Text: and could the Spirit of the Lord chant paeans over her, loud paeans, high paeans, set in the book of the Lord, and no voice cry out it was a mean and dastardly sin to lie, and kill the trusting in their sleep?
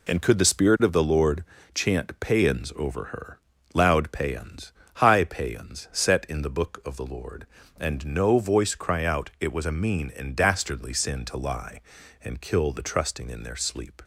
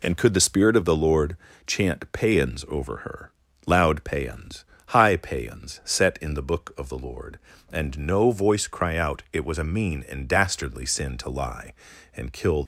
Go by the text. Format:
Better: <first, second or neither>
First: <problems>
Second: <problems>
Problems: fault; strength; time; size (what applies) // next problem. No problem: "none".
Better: first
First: pauses between "Lord" and "chant"; slight; at 1.4 s; 0.28 s long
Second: pauses between "Lord" and "chant"; slight; at 1.3 s; 0.28 s long // stops before "the trusting in their sleep"; at 12.6 s